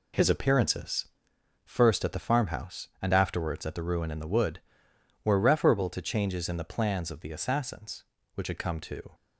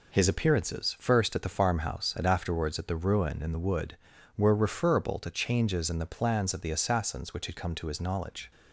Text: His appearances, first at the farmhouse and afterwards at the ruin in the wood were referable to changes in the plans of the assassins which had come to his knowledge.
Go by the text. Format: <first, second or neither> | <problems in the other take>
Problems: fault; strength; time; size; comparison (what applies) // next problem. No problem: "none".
second | stops before "his knowledge"; at 9.1 s